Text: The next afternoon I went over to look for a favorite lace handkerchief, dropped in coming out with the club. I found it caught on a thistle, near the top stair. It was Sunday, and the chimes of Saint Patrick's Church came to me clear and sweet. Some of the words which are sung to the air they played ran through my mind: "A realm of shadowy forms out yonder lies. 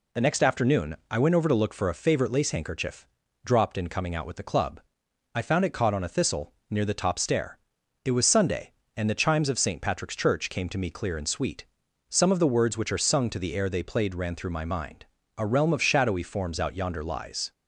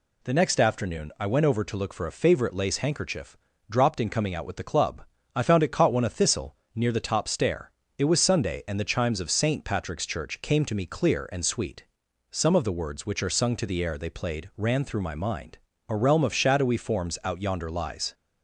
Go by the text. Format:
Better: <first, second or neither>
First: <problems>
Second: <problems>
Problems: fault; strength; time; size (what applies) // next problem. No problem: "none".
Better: first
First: none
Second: says "one" for "on"; at 5.9 s